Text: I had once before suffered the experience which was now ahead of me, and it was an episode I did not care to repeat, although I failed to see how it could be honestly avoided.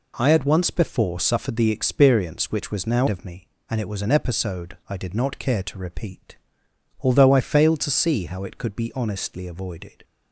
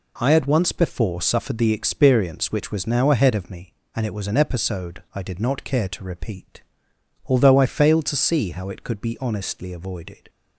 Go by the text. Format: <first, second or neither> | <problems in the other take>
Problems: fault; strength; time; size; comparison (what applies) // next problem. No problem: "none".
second | skips "ahead"; at 3.0 s